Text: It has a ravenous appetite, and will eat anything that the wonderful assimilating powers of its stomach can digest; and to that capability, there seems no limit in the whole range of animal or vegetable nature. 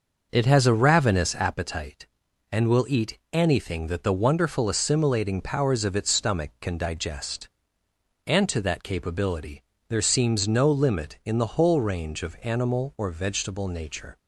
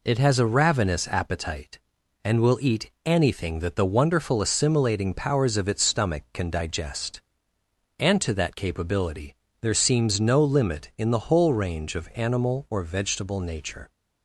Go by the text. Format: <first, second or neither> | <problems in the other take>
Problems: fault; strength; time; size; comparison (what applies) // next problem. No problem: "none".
second | starts louder than the rest; noticeable; until 1.5 s; 6 dB // pauses between "eat" and "anything"; slight; at 3.1 s; 0.16 s long; slight in the second